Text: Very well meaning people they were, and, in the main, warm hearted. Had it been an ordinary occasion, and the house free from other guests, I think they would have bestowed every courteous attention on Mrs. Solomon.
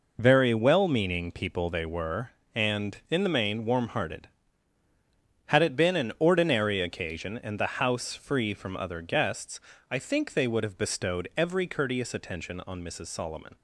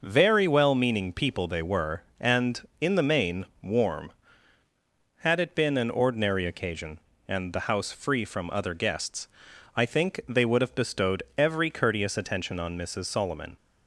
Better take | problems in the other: first | skips "hearted"; at 4.6 s

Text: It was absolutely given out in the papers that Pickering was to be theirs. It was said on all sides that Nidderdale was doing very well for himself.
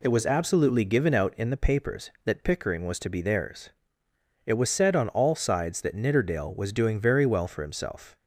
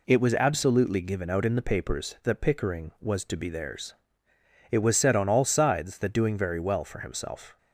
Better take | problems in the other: first | skips "Nidderdale was"; at 6.1 s

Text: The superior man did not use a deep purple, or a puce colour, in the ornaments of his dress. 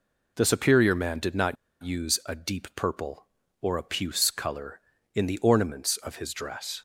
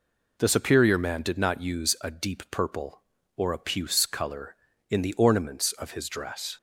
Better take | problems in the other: second | pauses between "not" and "use"; slight; at 1.5 s; 0.28 s long

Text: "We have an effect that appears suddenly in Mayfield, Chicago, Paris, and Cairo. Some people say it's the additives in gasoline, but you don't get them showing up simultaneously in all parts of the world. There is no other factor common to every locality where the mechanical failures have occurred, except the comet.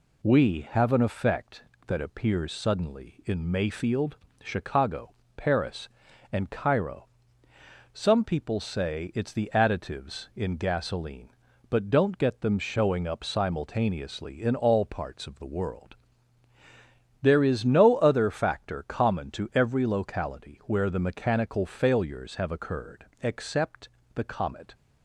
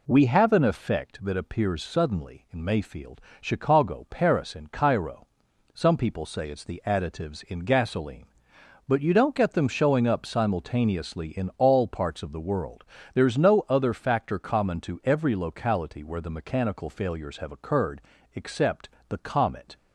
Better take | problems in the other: second | skips "you"; at 11.8 s // pauses between "except" and "the"; slight; at 23.8 s; 0.28 s long; slight in the second

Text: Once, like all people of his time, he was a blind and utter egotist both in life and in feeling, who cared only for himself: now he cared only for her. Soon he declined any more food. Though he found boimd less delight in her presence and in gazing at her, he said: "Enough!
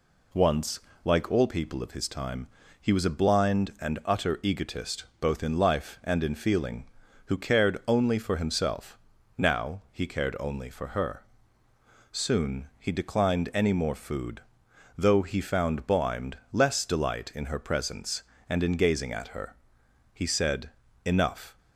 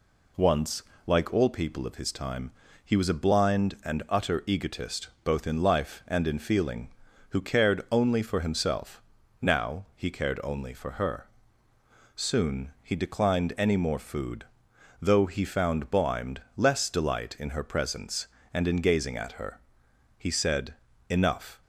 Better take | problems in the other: neither | pauses between "egotist" and "both"; slight; the same in both // pauses between "boimd" and "less"; slight; the same in both

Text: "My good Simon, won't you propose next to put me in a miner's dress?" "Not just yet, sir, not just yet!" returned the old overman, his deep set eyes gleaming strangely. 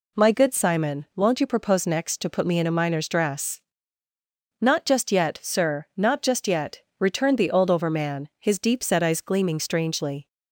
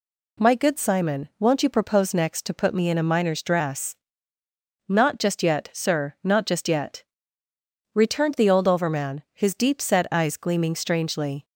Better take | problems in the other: neither | none

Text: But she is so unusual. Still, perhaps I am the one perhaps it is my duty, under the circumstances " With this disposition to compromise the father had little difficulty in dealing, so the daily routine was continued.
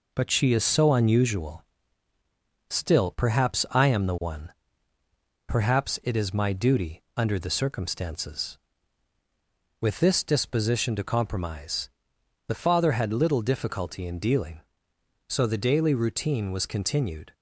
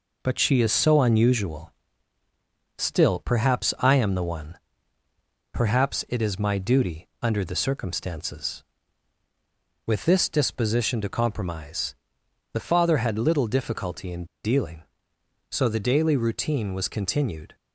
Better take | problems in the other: first | pauses between "one" and "perhaps"; noticeable; at 4.5 s; 0.96 s long; noticeable in the first // pauses between "compromise" and "the"; noticeable; at 11.9 s; 0.58 s long; noticeable in the first // pauses between "in" and "dealing"; slight; at 14.2 s; 0.19 s long

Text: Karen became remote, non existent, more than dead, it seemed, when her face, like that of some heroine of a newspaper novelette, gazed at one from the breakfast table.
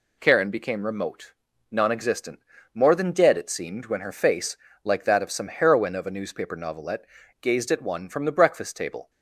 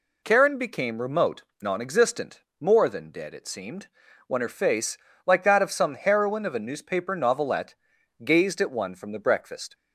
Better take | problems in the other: first | stops before "table"; at 9.7 s

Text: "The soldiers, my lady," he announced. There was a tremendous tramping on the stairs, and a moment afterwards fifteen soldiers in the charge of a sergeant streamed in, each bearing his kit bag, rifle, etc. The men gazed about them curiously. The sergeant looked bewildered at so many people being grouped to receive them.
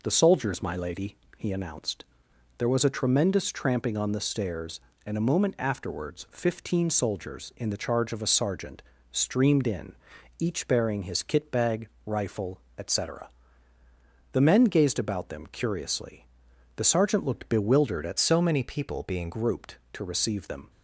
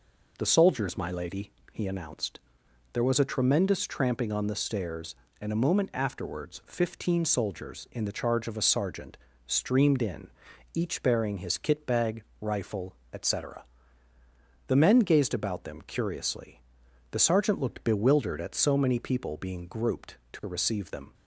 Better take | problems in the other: second | pauses between "sergeant" and "streamed"; slight; at 8.8 s; 0.30 s long; slight in the second // changes voice from "so" to "being"; from 18.1 to 19.2 s; 1.1 s long

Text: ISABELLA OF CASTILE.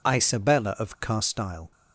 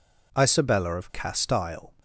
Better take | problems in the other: neither | none

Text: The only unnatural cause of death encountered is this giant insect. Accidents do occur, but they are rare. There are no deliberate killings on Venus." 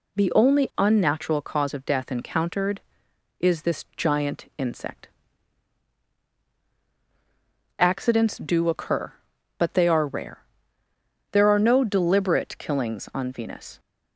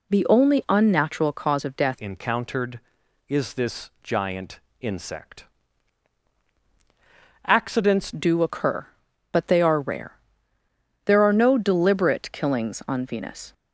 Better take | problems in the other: first | changes voice from "encountered" to "Accidents"; from 1.9 to 8.1 s; 6.2 s long // pauses between "giant" and "insect"; slight; at 4.5 s; 0.20 s long

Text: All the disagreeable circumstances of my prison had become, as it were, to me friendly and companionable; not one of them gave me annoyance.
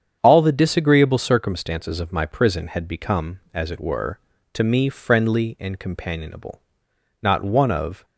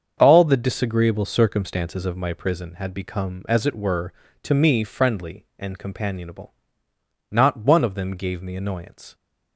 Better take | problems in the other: second | starts louder than the rest; strong; until 1.2 s; 8 dB; also in the second // stops before "them gave me annoyance"; at 8.0 s

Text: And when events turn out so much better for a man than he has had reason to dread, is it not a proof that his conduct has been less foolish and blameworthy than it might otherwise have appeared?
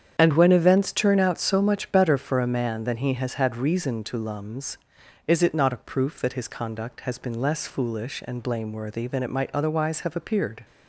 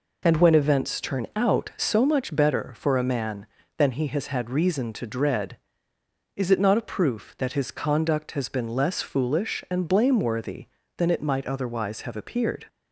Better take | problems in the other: second | starts louder than the rest; strong; until 1.1 s; 8 dB // says "lums" for "dread"; at 4.1 s

